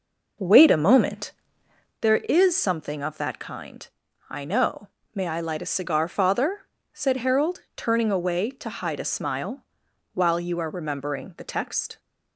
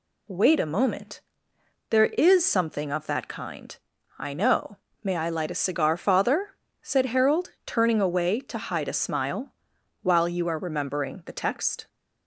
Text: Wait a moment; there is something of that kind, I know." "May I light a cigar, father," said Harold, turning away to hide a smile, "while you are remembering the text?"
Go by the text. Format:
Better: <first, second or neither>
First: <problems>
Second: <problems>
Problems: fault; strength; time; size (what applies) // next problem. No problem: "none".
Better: second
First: starts louder than the rest; noticeable; until 2.1 s; 5.5 dB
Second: none